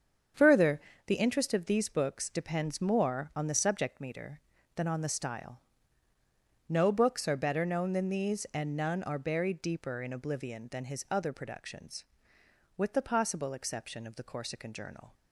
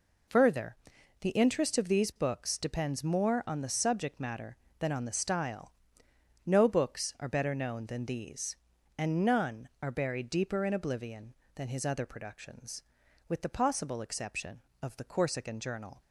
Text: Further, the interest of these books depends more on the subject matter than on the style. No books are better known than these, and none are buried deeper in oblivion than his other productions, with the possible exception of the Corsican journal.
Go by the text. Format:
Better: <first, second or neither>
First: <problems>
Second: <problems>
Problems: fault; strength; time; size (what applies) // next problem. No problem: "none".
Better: second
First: starts louder than the rest; strong; until 1.6 s; 7.5 dB // says "meter" for "matter"; at 4.0 s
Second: none